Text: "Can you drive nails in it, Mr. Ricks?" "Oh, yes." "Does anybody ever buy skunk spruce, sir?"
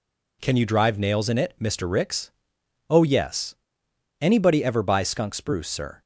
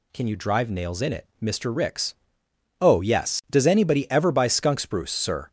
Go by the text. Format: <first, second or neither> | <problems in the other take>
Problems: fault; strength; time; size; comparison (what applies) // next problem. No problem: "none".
second | skips "Does"; at 3.8 s